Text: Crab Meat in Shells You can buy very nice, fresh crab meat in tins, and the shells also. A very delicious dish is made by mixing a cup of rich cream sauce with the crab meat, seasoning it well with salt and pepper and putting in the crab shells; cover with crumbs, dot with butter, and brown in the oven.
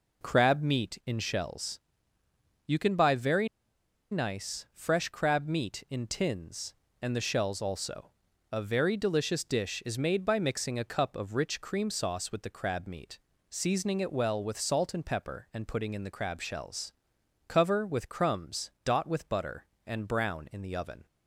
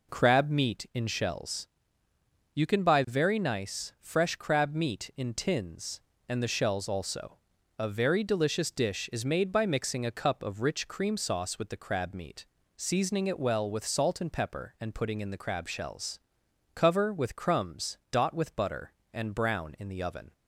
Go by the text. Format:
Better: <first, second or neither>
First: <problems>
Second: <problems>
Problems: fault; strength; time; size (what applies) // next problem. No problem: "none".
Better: second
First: pauses between "Shells" and "You"; noticeable; at 1.7 s; 0.86 s long // pauses between "very" and "nice"; noticeable; at 3.4 s; 0.63 s long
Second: pauses between "Shells" and "You"; noticeable; at 1.6 s; 0.86 s long